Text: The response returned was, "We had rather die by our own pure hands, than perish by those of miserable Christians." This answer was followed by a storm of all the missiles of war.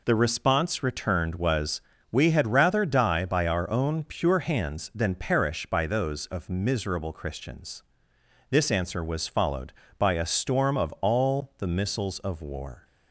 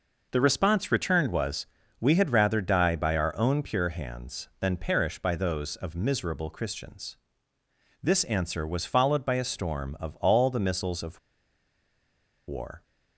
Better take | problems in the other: first | pauses between "of" and "war"; strong; at 11.1 s; 1.2 s long

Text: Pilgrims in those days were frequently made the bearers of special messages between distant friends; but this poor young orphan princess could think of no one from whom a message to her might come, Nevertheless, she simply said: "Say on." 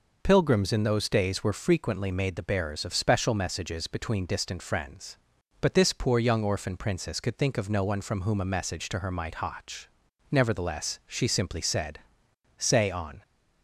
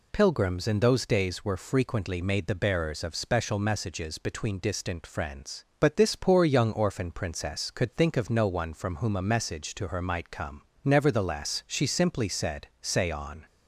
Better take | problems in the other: second | says "hotch" for "come"; at 9.3 s

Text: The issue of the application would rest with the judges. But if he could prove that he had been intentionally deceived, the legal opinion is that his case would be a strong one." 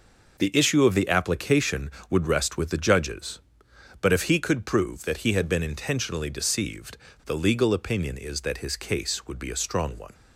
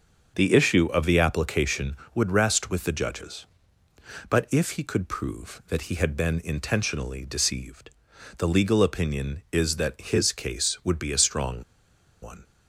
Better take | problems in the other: first | starts louder than the rest; until 1.3 s; 7 dB // pauses between "strong" and "one"; noticeable; at 11.6 s; 0.60 s long

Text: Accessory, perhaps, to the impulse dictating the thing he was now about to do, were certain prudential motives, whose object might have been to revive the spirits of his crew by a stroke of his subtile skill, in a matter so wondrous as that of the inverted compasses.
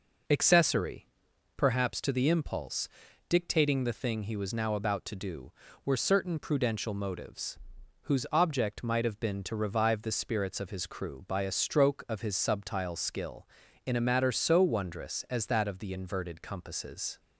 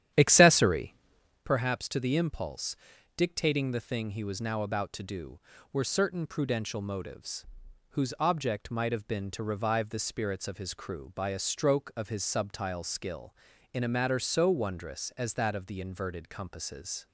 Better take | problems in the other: first | starts louder than the rest; strong; until 1.4 s; 10.5 dB // pauses between "impulse" and "dictating"; at 2.7 s; 0.42 s long; also in the first

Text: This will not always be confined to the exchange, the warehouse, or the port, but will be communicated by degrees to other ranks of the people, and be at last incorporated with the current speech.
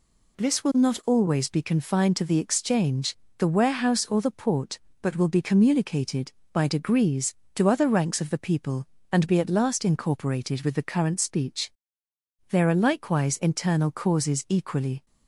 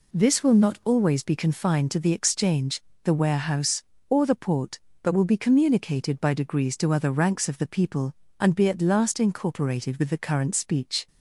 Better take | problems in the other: second | goes on to say "There are likewise internal causes equally"; strong; from 12.4 s on; 2.5 s long

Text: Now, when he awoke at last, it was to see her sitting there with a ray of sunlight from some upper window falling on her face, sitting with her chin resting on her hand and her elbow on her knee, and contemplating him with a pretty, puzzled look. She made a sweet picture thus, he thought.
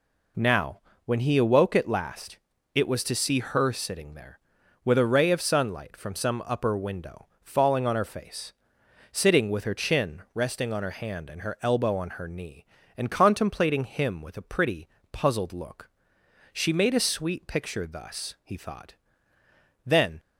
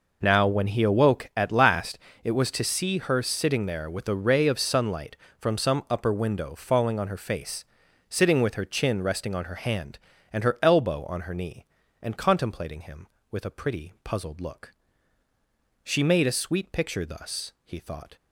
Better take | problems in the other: second | pauses between "window" and "falling"; slight; at 7.2 s; 0.16 s long // goes on to say "Then"; slight; from 19.8 s on; 0.34 s long

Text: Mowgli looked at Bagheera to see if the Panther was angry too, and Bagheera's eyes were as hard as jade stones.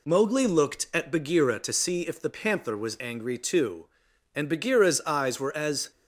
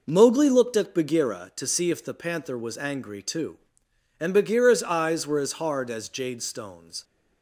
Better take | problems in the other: second | stops before "hard as jade stones"; at 5.9 s

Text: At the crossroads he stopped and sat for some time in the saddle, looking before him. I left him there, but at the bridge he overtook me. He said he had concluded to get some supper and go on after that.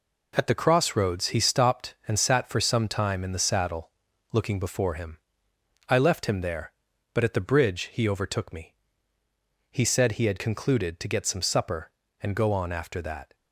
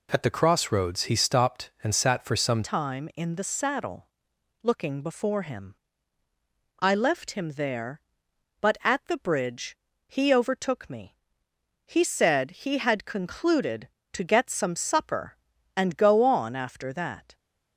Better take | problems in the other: first | changes voice at "time"; from 2.6 s on; 14.7 s long // pauses between "bridge" and "he"; slight; at 9.7 s; 0.30 s long

